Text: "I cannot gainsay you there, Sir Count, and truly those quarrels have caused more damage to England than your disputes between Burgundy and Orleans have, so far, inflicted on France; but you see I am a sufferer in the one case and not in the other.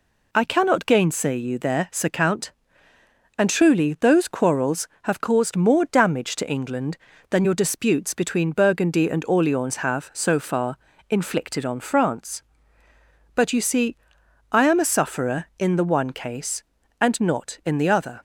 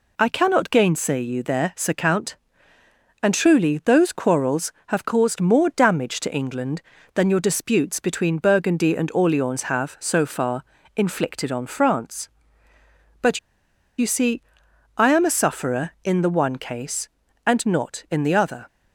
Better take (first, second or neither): first